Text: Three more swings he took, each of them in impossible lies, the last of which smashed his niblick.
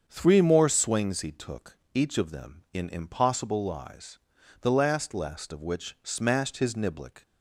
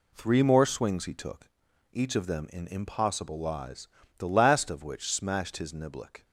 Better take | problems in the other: second | starts louder than the rest; strong; until 1.0 s; 7 dB // says "last" twice; at 5.1 s

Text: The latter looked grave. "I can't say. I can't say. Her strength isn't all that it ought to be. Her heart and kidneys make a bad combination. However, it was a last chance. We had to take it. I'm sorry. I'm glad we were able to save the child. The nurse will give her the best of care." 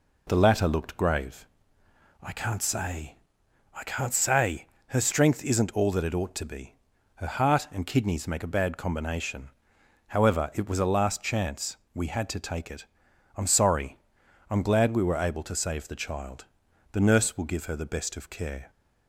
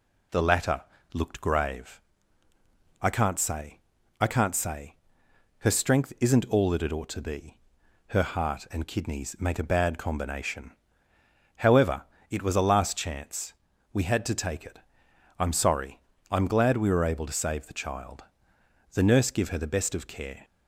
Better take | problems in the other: first | pauses between "latter" and "looked"; slight; at 0.8 s; 0.32 s long // skips "will"; at 19.3 s

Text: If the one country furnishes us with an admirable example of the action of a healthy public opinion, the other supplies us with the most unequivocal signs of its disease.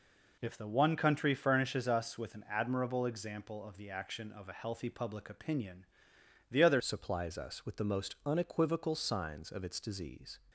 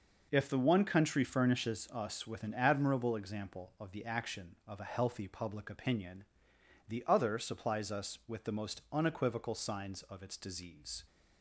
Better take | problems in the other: second | changes voice at "supplies"; from 6.7 s on; 3.6 s long

